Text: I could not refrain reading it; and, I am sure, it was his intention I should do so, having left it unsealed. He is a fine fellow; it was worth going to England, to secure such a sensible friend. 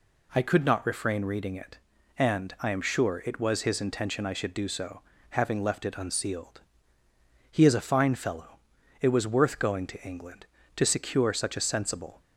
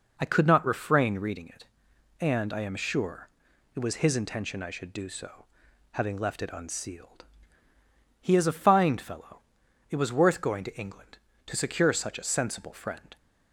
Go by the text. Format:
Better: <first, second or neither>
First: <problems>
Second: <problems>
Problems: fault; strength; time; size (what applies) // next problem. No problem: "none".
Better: second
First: stops before "friend"; at 12.2 s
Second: none